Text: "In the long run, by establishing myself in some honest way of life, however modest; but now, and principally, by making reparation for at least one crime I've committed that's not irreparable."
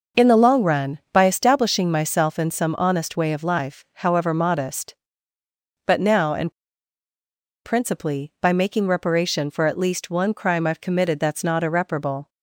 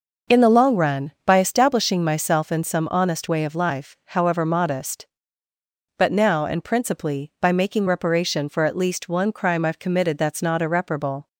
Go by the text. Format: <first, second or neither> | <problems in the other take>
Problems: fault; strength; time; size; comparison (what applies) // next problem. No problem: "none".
second | pauses between "and" and "principally"; at 6.5 s; 1.1 s long